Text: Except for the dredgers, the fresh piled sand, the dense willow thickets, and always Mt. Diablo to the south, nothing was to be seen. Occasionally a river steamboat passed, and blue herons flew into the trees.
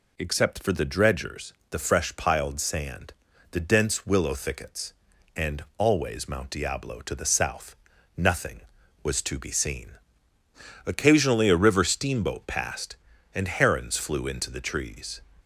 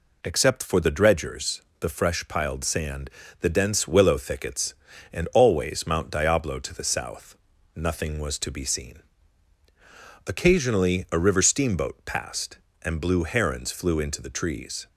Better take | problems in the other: second | skips "blue"; at 13.4 s

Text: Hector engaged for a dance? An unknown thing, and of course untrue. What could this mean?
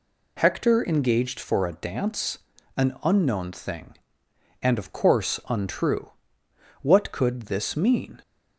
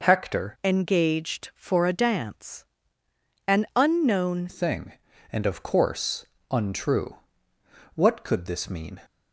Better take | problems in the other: first | changes voice from "engaged" to "unknown"; from 0.6 to 4.4 s; 3.8 s long // pauses between "course" and "untrue"; slight; at 6.2 s; 0.28 s long

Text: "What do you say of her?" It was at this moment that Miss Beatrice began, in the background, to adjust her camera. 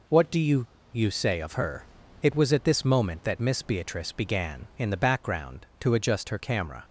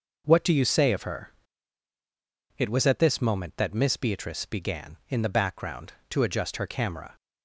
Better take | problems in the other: second | says "you" twice; at 0.9 s

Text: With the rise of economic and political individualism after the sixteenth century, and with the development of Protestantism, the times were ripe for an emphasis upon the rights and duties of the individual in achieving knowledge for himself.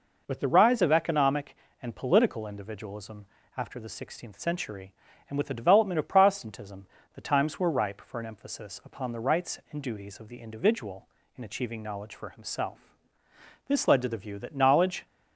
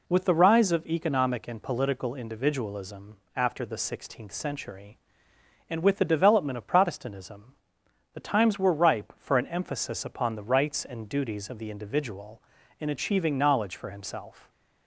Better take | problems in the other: second | pauses between "individualism" and "after"; slight; at 3.2 s; 0.30 s long; slight in the second // goes on to say "This led to the view that knowledge"; from 13.6 s on; 1.3 s long

